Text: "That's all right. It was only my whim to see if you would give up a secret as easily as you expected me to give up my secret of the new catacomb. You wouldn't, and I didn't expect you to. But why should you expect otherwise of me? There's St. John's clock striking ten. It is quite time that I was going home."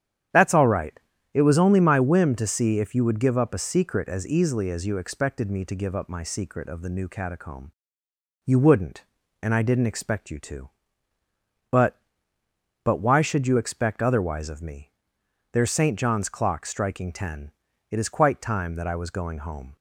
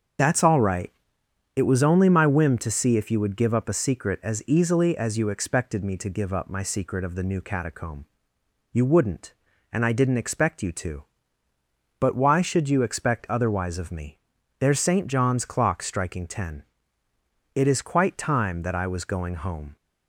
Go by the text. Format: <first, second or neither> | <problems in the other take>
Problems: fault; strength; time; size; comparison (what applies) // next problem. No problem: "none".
second | starts louder than the rest; strong; until 1.6 s; 9.5 dB; also in the second // says "But" twice; at 12.8 s